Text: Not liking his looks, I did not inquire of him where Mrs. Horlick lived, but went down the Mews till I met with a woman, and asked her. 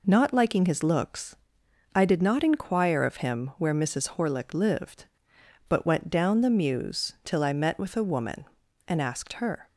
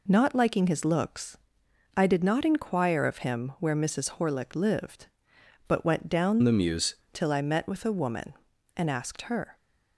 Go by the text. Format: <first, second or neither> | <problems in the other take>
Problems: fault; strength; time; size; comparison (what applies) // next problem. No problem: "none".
first | changes voice from "the" to "Mews"; from 6.4 to 6.9 s; 0.5 s long